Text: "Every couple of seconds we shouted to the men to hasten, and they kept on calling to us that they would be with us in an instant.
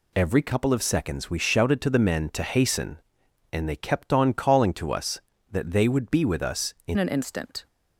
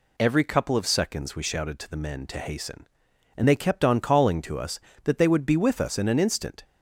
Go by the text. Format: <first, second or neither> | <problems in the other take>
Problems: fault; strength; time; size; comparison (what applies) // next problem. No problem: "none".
second | changes voice at "an"; from 6.9 s on; 0.7 s long